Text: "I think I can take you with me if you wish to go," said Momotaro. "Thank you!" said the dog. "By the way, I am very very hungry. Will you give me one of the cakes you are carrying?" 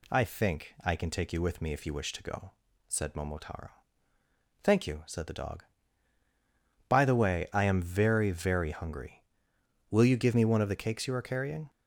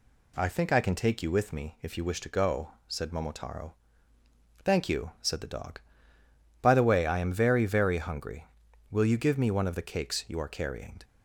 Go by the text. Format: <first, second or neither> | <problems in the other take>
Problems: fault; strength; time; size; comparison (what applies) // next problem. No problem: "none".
neither | none